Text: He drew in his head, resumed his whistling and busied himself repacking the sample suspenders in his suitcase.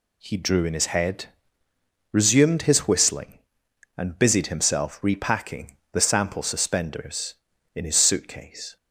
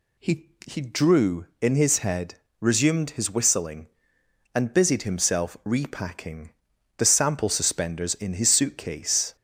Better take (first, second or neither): first